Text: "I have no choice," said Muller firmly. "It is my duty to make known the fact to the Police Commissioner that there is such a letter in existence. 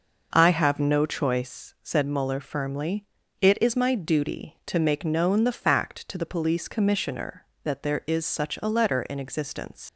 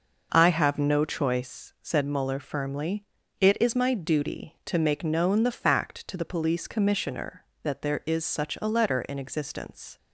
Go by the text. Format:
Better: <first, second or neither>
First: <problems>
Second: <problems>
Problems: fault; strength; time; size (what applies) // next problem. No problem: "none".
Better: second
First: leaves "existence" unfinished; at 9.8 s; 90 ms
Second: none